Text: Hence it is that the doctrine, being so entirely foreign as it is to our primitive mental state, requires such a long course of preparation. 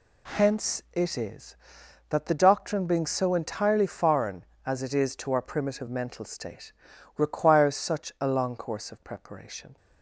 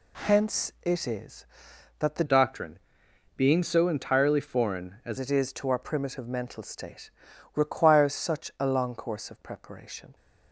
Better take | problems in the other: first | changes voice from "doctrine" to "as"; from 2.2 to 5.1 s; 2.9 s long

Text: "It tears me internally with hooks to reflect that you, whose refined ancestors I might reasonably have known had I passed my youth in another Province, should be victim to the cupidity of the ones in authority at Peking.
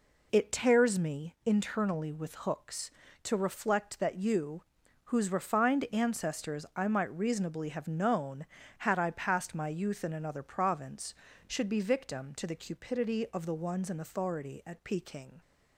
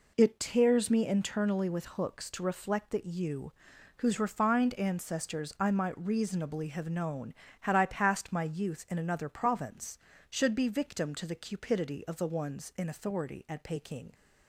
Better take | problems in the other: neither | none

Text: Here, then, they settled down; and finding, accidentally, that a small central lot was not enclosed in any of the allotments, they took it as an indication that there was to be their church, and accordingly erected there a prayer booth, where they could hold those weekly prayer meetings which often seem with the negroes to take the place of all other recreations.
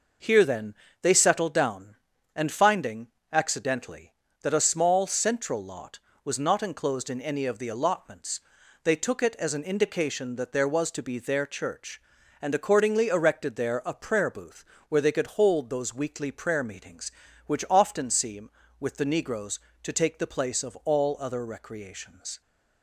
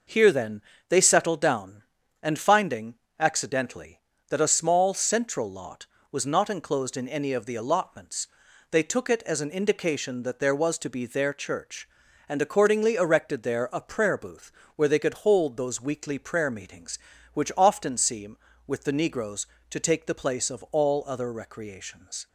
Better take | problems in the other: neither | none

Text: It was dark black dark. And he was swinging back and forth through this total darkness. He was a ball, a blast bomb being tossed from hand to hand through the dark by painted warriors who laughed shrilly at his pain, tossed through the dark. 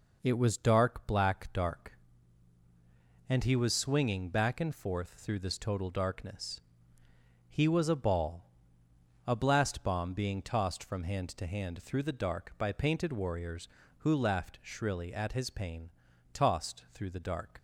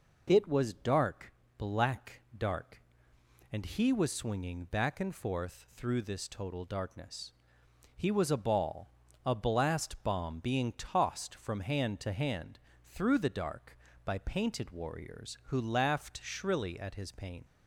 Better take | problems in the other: first | pauses between "dark" and "black"; slight; at 1.3 s; 0.24 s long // pauses between "black" and "dark"; slight; at 2.2 s; 0.16 s long // pauses between "hand" and "through"; slight; at 12.5 s; 0.28 s long // stops before "tossed through the dark"; at 17.4 s

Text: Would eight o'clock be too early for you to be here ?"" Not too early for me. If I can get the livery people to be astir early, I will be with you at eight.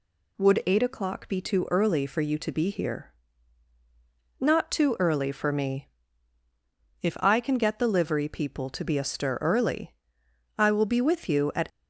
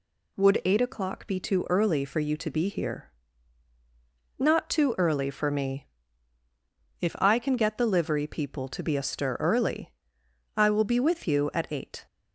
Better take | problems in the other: second | stops before "eight"; at 11.7 s

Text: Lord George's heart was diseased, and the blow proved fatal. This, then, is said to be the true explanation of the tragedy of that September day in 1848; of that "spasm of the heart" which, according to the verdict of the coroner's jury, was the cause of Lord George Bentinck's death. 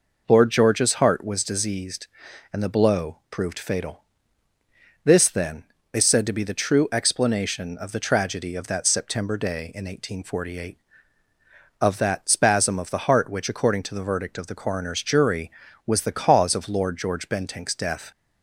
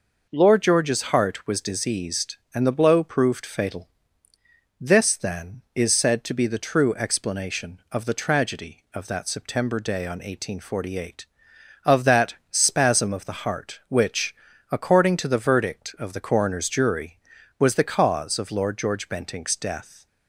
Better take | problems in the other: first | says "on" for "in"; at 10.0 s // pauses between "that" and "spasm"; slight; at 12.3 s; 0.16 s long

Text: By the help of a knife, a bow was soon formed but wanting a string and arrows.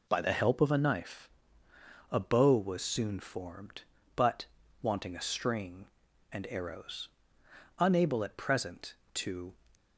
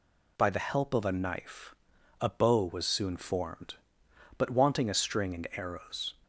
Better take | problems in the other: second | pauses between "but" and "wanting"; slight; at 4.4 s; 0.34 s long // goes on to say "Unable at present to"; strong; from 7.8 s on; 1.7 s long

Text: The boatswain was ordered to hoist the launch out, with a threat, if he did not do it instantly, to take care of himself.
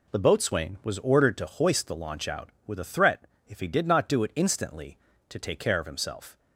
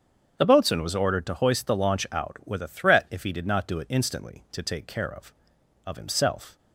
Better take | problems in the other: first | starts louder than the rest; strong; until 1.4 s; 8 dB // says "of" twice; at 5.8 s

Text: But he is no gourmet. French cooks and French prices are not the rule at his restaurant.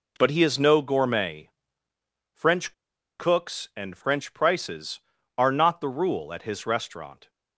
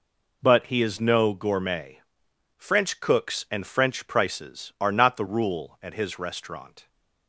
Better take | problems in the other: second | pauses between "French" and "cooks"; noticeable; at 2.7 s; 0.46 s long

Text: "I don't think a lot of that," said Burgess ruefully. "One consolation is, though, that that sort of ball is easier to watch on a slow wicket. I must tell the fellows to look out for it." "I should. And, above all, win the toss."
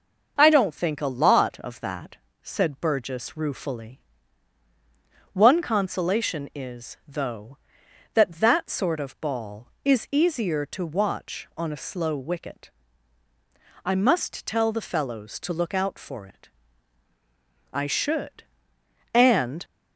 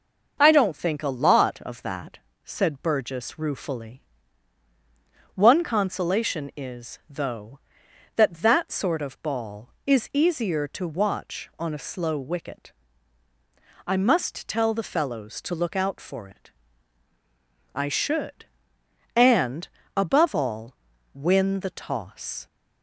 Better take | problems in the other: second | starts louder than the rest; noticeable; until 1.3 s; 6 dB; noticeable in the second // stops before "above all win the toss"; at 19.6 s

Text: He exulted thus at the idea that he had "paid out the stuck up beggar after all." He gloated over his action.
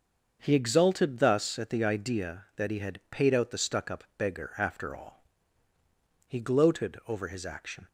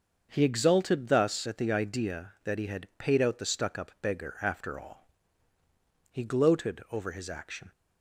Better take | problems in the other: neither | starts louder than the rest; the same in both

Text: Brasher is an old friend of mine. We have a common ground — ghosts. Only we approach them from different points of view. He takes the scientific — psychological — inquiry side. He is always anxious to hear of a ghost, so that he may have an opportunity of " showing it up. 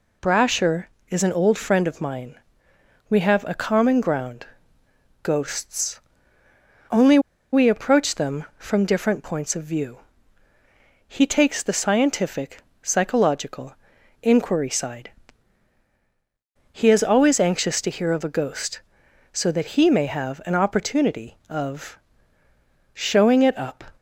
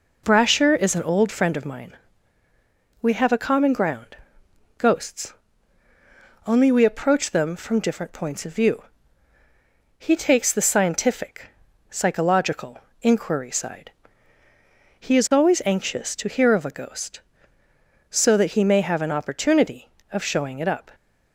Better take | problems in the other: second | pauses between "Only" and "we"; slight; at 7.1 s; 0.34 s long

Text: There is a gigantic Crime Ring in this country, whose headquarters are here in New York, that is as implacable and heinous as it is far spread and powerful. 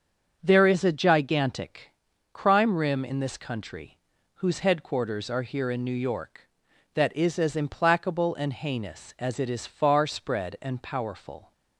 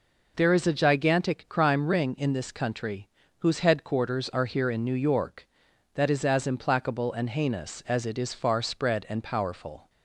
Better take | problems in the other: second | starts louder than the rest; until 1.4 s; 7 dB // pauses between "gigantic" and "Crime"; at 1.8 s; 0.42 s long // says "Rim" for "Ring"; at 2.7 s

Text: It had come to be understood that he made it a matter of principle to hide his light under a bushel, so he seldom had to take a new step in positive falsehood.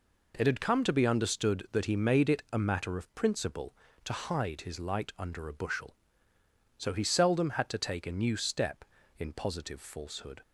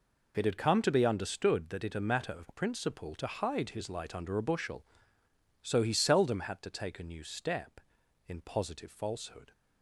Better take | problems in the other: first | skips "he made"; at 1.8 s

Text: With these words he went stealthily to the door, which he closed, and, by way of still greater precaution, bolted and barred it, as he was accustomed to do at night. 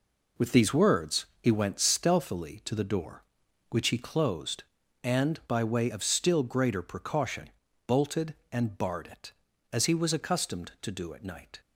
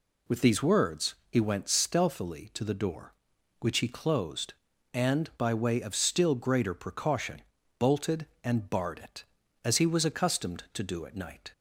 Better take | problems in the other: second | gets quieter; strong; throughout; 8 dB // pauses between "words" and "he"; slight; at 1.2 s; 0.16 s long; slight in the second

